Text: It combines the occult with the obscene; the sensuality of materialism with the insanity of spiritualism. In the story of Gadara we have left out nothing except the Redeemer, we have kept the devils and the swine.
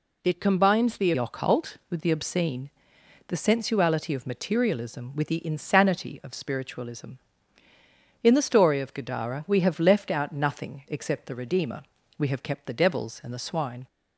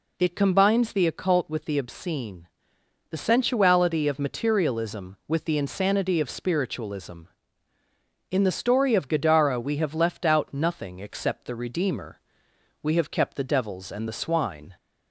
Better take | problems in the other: second | changes voice at "occult"; from 1.1 s on; 12.7 s long

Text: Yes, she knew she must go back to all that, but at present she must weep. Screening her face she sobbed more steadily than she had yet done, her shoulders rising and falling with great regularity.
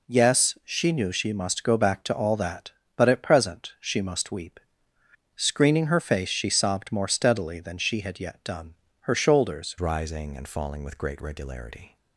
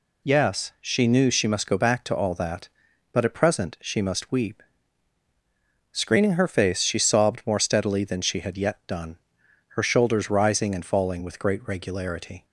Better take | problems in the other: second | changes voice at "rising"; from 9.7 s on; 2.2 s long

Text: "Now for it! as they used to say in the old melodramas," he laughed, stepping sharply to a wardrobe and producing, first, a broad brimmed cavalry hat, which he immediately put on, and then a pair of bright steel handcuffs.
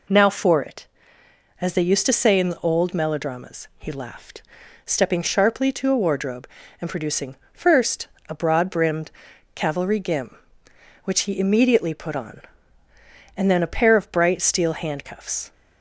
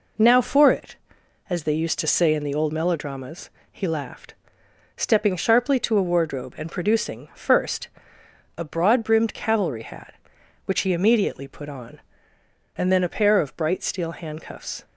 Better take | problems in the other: second | pauses between "brimmed" and "cavalry"; at 9.1 s; 0.42 s long // says "gim" for "hat"; at 9.9 s

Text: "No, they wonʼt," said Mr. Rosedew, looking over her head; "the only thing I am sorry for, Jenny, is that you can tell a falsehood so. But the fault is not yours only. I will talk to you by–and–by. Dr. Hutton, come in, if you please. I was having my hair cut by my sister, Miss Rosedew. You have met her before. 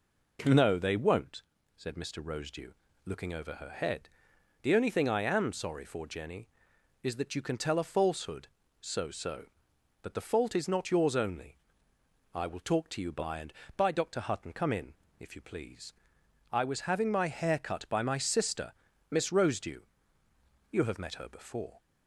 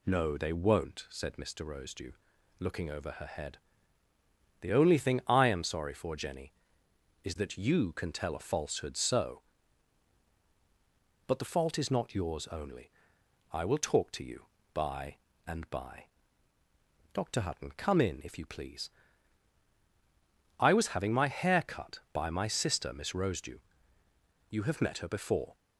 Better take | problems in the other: second | says "so" twice; at 9.1 s

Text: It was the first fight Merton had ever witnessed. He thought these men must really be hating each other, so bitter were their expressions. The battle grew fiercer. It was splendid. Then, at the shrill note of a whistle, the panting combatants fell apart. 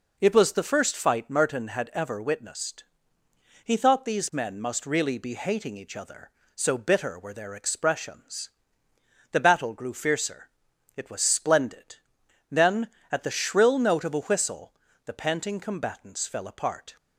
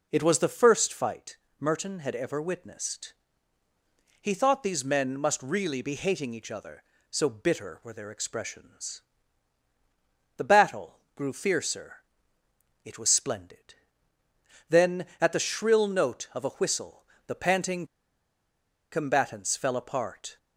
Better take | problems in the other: first | pauses between "fight" and "Merton"; slight; at 1.3 s; 0.24 s long // pauses between "battle" and "grew"; slight; at 10.9 s; 0.16 s long // pauses between "panting" and "combatants"; at 17.8 s; 1.0 s long

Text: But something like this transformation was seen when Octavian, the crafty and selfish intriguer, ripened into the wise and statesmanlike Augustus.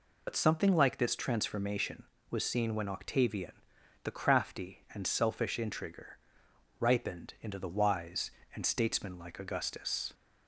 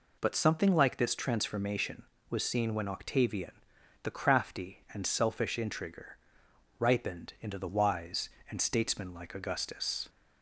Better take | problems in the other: second | loses the start of "But"; at 0.2 s; 70 ms

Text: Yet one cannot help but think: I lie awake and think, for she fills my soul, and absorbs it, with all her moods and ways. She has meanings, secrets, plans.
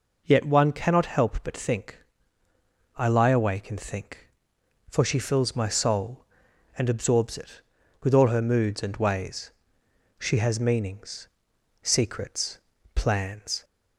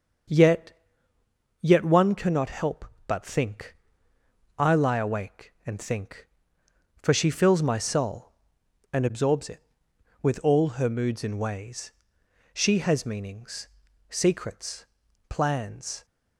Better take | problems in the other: first | starts louder than the rest; until 2.1 s; 6.5 dB // says "Yet" twice; at 1.6 s

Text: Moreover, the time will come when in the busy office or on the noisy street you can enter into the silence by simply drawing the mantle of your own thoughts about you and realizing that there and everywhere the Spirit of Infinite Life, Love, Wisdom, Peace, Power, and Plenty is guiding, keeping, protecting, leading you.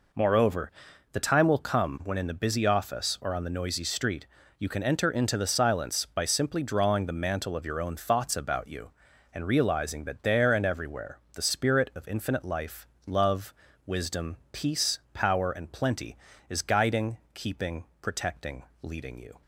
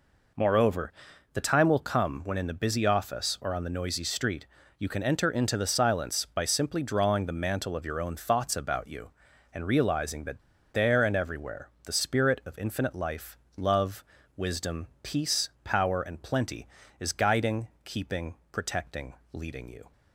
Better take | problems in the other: first | pauses between "street" and "you"; slight; at 4.4 s; 0.34 s long; slight in the first // pauses between "that" and "there"; slight; at 10.4 s; 0.32 s long // pauses between "everywhere" and "the"; slight; at 11.6 s; 0.16 s long; slight in the first

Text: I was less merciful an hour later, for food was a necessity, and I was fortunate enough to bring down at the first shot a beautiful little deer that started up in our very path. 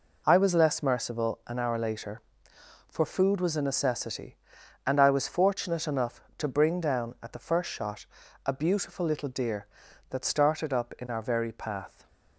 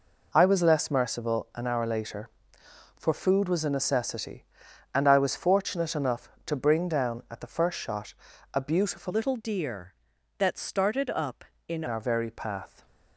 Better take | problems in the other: first | pauses between "shot" and "a"; at 8.1 s; 0.40 s long; also in the first // changes voice from "little" to "in"; from 9.0 to 11.8 s; 2.8 s long

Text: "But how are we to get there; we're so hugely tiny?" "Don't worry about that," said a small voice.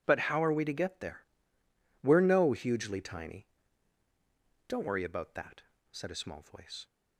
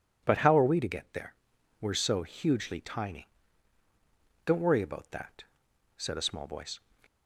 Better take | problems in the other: second | says "no" for "so"; at 2.1 s

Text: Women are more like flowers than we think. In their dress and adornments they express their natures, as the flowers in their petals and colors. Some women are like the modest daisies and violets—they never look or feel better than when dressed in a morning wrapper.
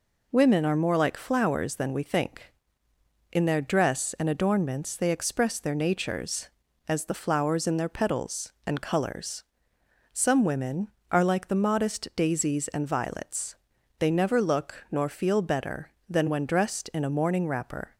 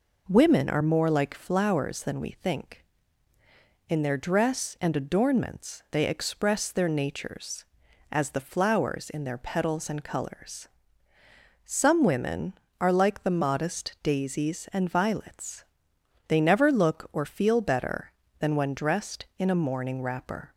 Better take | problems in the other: second | says "nor" for "or"; at 14.9 s

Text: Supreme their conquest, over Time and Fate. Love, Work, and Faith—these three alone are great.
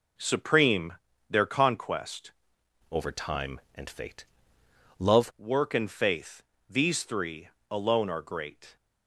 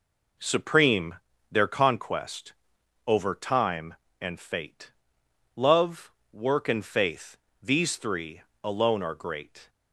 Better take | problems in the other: second | pauses between "Supreme" and "their"; slight; at 0.9 s; 0.34 s long; slight in the second // changes voice from "over" to "Love"; from 2.9 to 5.3 s; 2.4 s long // pauses between "three" and "alone"; slight; at 7.4 s; 0.20 s long; slight in the second

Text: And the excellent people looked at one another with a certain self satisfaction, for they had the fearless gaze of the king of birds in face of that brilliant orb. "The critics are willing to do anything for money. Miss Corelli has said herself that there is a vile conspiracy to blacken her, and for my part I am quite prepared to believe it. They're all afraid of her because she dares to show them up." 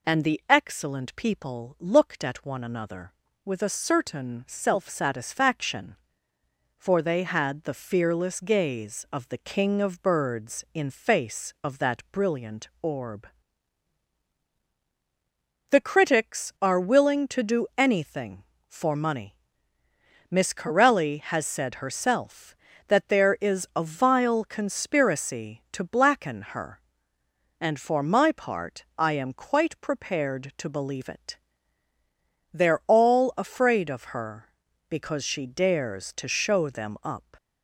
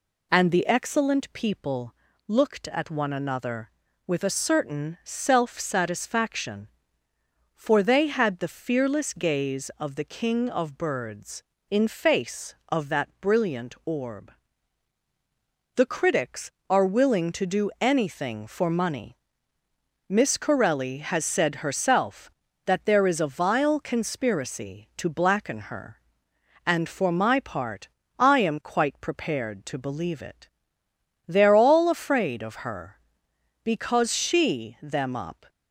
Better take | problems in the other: first | pauses between "people" and "looked"; slight; at 1.9 s; 0.34 s long // pauses between "part" and "I"; slight; at 27.8 s; 0.32 s long // skips "dares to show"; at 34.7 s

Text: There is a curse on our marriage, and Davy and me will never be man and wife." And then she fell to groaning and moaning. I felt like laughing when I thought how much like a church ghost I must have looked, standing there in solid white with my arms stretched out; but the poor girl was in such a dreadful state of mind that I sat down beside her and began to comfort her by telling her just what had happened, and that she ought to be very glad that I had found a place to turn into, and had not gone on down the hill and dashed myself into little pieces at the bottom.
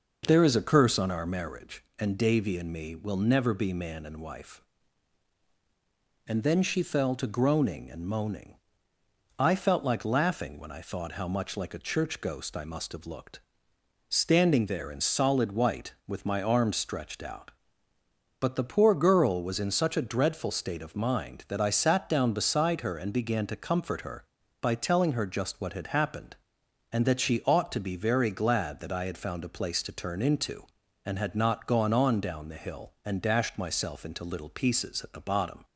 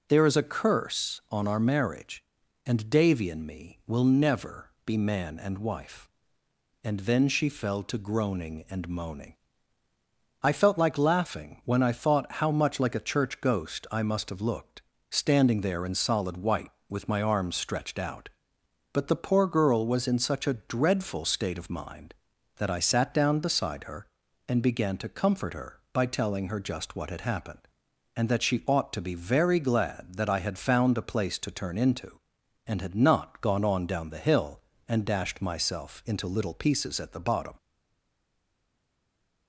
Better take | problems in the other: first | pauses between "never" and "be"; slight; at 4.6 s; 0.16 s long // stays silent after the last word; noticeable; from 37.5 s on; 1.9 s long

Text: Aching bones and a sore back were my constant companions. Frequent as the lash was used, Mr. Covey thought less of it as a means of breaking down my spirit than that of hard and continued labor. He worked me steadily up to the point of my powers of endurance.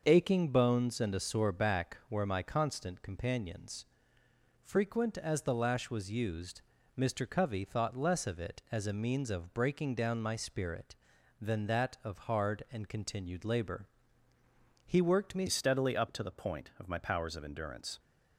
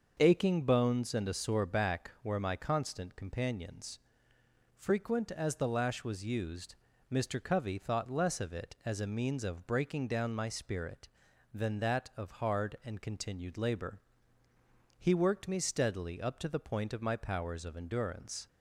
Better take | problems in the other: second | starts louder than the rest; until 1.0 s; 6.5 dB; also in the second // changes voice at "steadily"; from 15.4 s on; 2.5 s long

